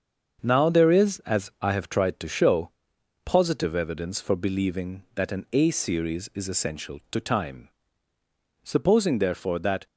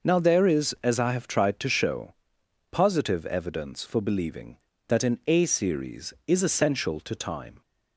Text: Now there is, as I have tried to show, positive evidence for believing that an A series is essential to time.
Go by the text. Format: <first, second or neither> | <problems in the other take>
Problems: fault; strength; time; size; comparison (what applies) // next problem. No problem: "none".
second | starts louder than the rest; until 1.4 s; 6.5 dB // goes on to say "Supposing therefore that"; noticeable; from 8.6 s on; 1.2 s long